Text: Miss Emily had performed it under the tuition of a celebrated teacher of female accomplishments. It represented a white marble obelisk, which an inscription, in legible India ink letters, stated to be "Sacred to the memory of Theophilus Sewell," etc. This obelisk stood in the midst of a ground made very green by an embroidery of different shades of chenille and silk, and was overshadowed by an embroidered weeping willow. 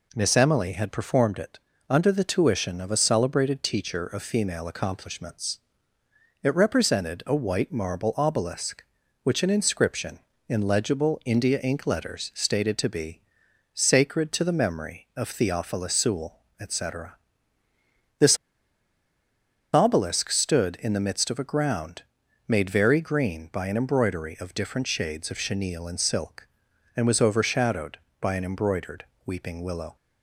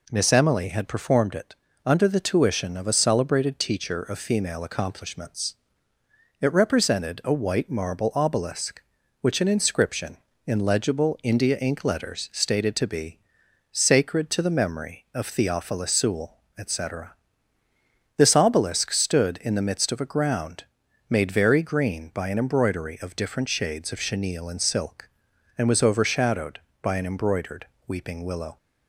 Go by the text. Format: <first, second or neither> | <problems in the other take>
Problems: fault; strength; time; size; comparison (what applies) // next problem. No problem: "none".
second | pauses between "it" and "under"; slight; at 1.5 s; 0.30 s long; slight in the second // pauses between "be" and "Sacred"; noticeable; at 13.2 s; 0.54 s long; noticeable in the second // pauses between "This" and "obelisk"; strong; at 18.3 s; 1.3 s long // pauses between "ground" and "made"; noticeable; at 22.0 s; 0.46 s long; noticeable in the second // pauses between "embroidered" and "weeping"; slight; at 29.0 s; 0.22 s long; slight in the second